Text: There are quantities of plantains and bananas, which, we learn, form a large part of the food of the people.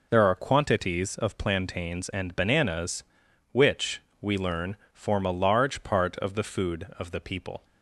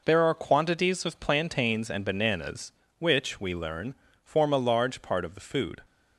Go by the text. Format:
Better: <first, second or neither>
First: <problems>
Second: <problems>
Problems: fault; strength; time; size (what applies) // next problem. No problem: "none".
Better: first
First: none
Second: stops before "of the people"; at 5.8 s